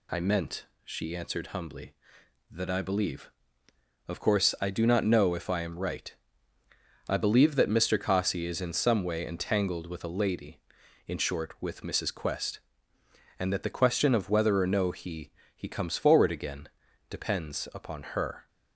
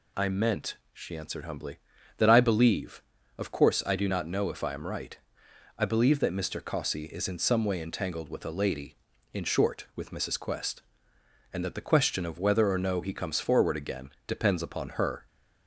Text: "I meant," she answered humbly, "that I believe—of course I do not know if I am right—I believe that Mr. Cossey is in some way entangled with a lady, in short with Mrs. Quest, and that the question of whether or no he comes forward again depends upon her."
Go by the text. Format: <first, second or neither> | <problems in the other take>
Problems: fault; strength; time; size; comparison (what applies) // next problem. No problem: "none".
second | says "he" twice; at 15.5 s // pauses between "again" and "depends"; at 16.6 s; 0.40 s long; slight in the second